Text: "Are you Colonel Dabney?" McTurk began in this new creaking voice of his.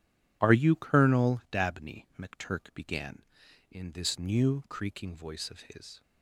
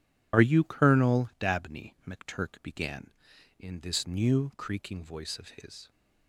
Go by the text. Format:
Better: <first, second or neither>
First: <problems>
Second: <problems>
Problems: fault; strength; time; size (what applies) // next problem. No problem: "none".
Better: first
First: none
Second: loses the start of "Are"; at 0.3 s; 45 ms